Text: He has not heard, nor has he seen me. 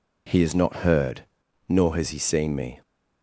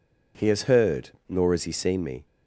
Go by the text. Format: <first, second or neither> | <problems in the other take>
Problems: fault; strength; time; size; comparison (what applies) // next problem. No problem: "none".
first | skips "not"; at 0.6 s